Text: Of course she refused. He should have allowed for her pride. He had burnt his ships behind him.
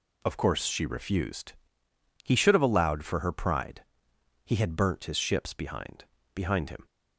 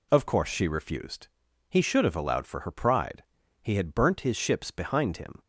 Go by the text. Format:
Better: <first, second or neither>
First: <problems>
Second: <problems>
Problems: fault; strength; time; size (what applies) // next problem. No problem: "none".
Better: second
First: says "behind" twice; at 6.3 s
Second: none